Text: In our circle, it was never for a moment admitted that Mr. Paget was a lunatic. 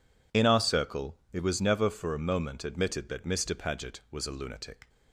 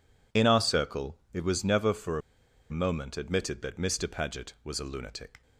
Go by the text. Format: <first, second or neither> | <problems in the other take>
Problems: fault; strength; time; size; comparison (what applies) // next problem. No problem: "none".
first | pauses between "a" and "moment"; noticeable; at 2.2 s; 0.50 s long